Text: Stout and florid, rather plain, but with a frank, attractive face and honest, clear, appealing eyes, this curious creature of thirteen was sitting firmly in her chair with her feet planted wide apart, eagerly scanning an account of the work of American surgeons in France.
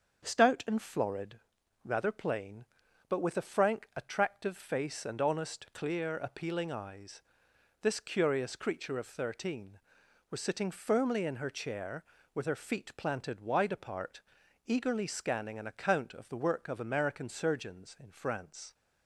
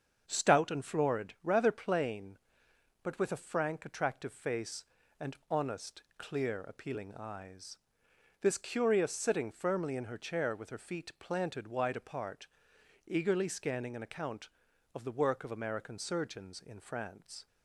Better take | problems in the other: first | starts louder than the rest; until 1.2 s; 7 dB; also in the first // skips "creature of thirteen was"; at 9.1 s

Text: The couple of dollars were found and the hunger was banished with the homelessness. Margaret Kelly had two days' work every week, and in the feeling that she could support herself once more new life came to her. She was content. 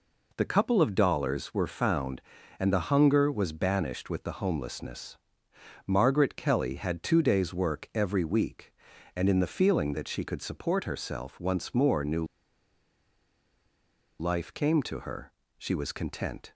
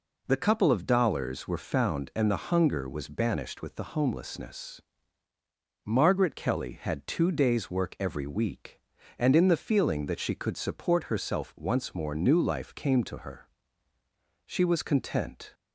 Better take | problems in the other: second | pauses between "new" and "life"; strong; at 12.2 s; 1.9 s long

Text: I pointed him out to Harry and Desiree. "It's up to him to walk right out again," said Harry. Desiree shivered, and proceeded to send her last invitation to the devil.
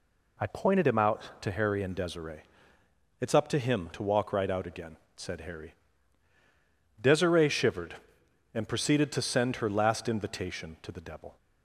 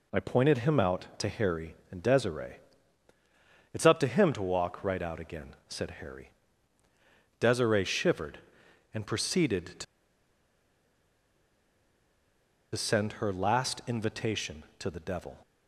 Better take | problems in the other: first | pauses between "to" and "send"; strong; at 9.8 s; 2.9 s long

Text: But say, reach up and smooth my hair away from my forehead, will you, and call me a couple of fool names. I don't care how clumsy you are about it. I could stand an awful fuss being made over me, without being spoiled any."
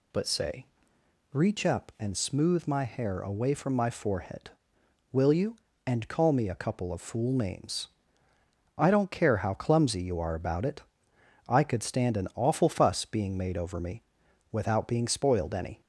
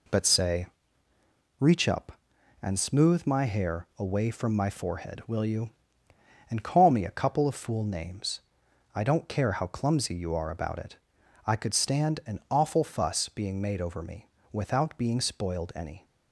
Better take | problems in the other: neither | none

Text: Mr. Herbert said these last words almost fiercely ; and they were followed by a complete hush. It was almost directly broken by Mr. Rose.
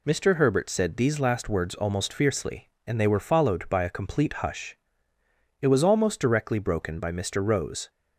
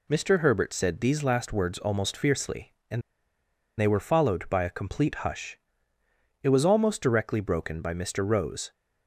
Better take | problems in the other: first | pauses between "and" and "they"; noticeable; at 3.0 s; 0.76 s long

